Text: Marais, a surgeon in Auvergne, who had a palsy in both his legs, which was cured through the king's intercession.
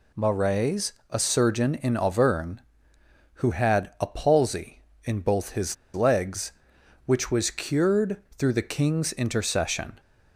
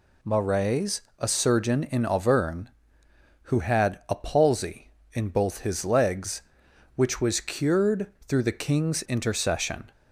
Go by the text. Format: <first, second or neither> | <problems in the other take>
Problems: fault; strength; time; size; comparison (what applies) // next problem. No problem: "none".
second | pauses between "his" and "legs"; slight; at 5.7 s; 0.19 s long // pauses between "cured" and "through"; slight; at 8.1 s; 0.20 s long; slight in the second